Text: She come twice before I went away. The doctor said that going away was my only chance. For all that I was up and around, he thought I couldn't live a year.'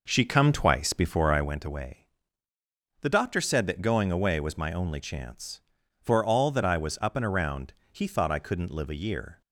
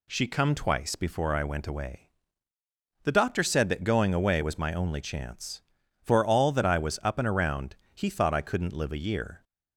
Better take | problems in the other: second | starts louder than the rest; noticeable; until 1.6 s; 5 dB

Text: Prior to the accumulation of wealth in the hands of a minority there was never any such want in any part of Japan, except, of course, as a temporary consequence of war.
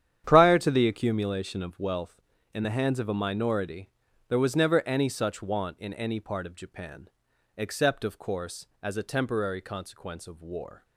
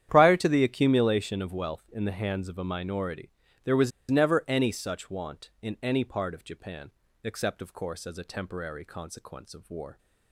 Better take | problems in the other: first | starts louder than the rest; strong; until 1.1 s; 10 dB; strong in the first // pauses between "minority" and "there"; slight; at 3.2 s; 0.34 s long; also in the first // pauses between "was" and "never"; slight; at 3.9 s; 0.20 s long

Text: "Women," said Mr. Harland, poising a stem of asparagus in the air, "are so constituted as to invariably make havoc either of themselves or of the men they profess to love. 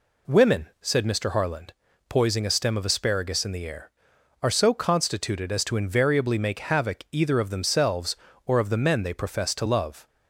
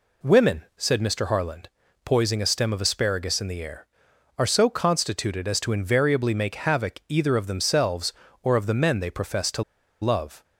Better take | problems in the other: first | pauses between "to" and "love"; at 9.6 s; 0.38 s long

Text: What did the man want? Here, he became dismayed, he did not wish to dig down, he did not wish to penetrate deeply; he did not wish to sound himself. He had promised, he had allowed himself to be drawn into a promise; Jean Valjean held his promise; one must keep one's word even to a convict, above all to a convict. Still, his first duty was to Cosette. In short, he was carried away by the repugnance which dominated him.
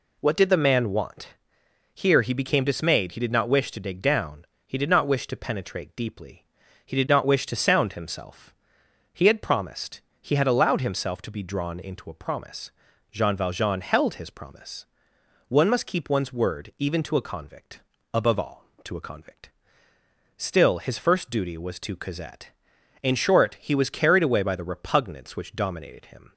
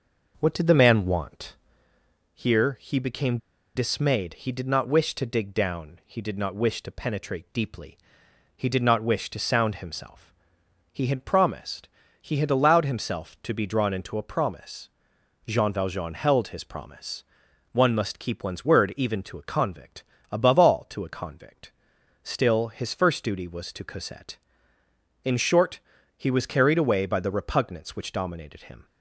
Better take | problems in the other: first | pauses between "became" and "dismayed"; at 3.3 s; 0.37 s long

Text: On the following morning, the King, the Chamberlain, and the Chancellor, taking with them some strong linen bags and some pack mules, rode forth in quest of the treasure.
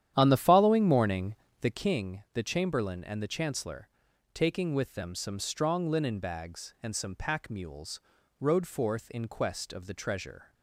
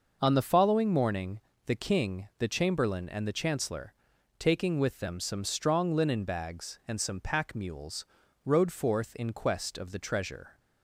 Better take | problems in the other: second | starts louder than the rest; strong; until 1.8 s; 10.5 dB

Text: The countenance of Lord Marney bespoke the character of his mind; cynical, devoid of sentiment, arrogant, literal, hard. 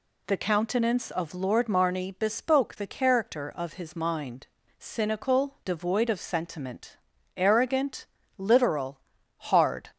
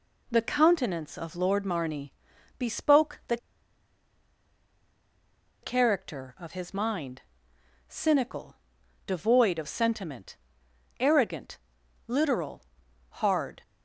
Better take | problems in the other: first | pauses between "Marney" and "bespoke"; noticeable; at 2.1 s; 0.46 s long // pauses between "the" and "character"; strong; at 3.3 s; 2.2 s long

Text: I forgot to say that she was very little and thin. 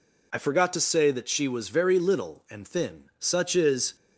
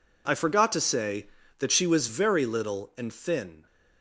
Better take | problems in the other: second | goes on to say "Such is"; noticeable; from 3.1 s on; 0.76 s long

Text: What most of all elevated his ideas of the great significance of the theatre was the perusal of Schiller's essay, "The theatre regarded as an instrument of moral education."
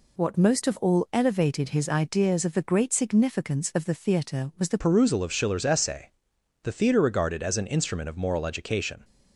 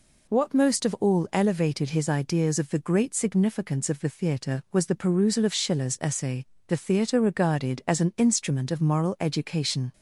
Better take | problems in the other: second | changes voice at "perusal"; from 4.7 s on; 4.3 s long

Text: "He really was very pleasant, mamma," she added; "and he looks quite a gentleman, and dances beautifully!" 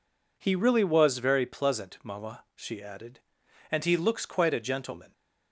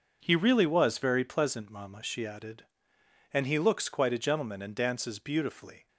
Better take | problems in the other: second | stops before "and dances beautifully"; at 5.1 s

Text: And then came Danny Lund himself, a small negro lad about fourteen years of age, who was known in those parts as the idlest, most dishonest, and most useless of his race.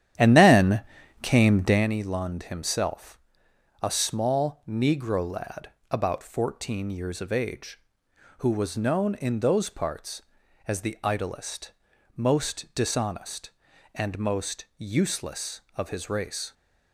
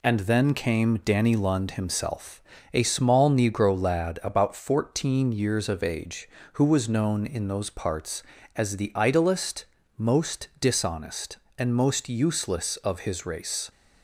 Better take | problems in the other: second | starts louder than the rest; strong; until 1.9 s; 10.5 dB // pauses between "then" and "came"; at 0.8 s; 0.40 s long // pauses between "lad" and "about"; slight; at 5.6 s; 0.20 s long

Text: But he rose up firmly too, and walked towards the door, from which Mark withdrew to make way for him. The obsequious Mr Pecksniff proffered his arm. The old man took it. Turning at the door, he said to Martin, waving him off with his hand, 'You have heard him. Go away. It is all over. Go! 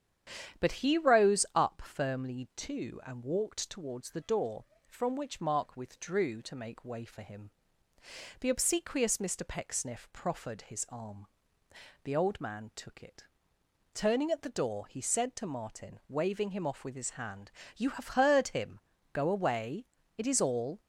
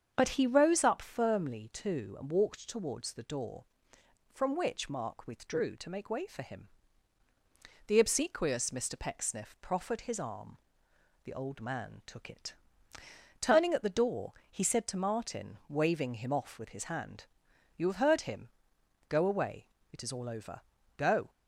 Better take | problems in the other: second | starts louder than the rest; strong; until 1.6 s; 9.5 dB; strong in the second // stops before "over Go"; at 20.7 s

